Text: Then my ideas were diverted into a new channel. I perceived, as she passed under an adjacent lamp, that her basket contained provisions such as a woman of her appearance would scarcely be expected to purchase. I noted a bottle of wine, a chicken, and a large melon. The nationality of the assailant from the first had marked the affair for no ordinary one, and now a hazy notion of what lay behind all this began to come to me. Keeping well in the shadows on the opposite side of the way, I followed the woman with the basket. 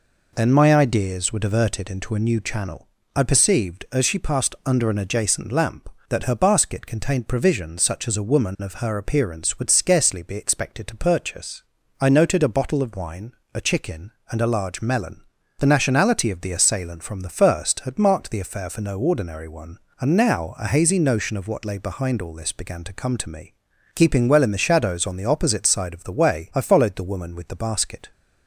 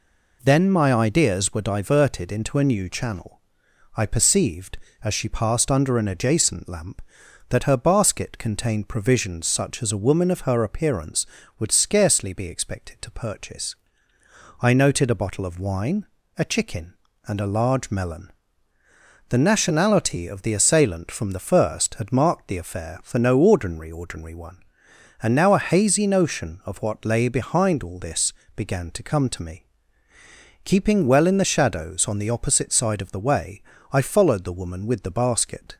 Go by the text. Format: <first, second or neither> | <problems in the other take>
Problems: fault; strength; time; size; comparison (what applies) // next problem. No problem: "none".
first | says "ordinary" twice; at 23.9 s // pauses between "this" and "began"; slight; at 28.3 s; 0.22 s long